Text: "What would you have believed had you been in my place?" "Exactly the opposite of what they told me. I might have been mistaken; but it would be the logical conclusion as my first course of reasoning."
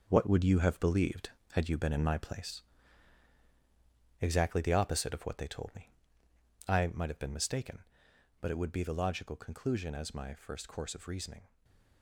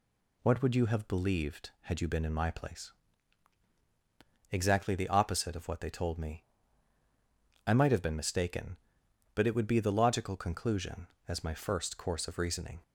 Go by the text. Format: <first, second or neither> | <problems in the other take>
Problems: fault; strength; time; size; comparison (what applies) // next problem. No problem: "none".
second | gets quieter; strong; throughout; 8.5 dB // stays silent after the last word; slight; from 11.4 s on; 0.6 s long